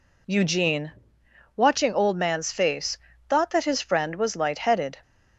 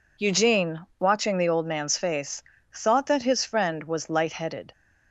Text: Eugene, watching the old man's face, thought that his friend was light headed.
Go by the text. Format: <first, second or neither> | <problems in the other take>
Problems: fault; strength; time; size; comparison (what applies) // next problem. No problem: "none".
second | skips "the"; at 1.9 s